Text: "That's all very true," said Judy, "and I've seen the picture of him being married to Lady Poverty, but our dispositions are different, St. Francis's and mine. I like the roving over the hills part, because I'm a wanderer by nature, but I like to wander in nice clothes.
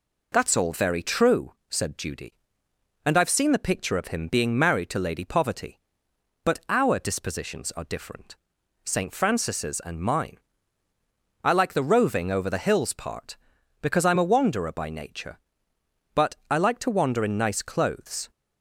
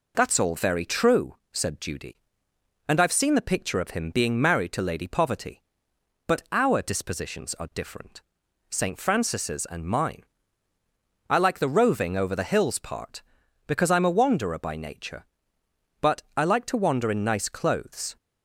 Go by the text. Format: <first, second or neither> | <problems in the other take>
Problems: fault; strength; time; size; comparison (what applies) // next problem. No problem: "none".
neither | none